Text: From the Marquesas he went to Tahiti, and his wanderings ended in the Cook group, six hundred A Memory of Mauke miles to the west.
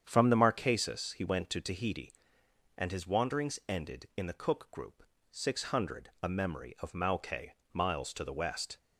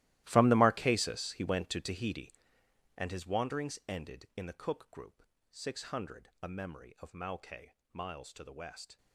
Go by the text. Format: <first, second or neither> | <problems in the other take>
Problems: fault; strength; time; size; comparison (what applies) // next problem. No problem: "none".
first | gets quieter; strong; throughout; 16 dB // starts louder than the rest; strong; until 1.2 s; 16 dB; strong in the first // pauses between "Mauke" and "miles"; slight; at 7.7 s; 0.20 s long; slight in the first